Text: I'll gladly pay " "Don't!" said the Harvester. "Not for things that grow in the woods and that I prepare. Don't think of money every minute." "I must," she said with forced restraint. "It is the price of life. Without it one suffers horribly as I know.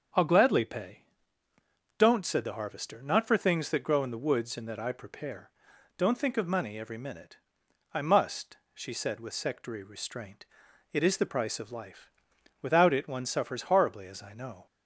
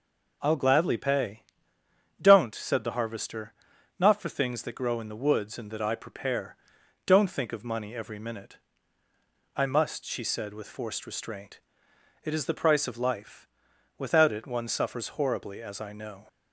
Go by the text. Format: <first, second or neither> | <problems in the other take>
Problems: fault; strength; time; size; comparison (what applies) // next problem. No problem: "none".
second | says "sectary" for "forced"; at 9.3 s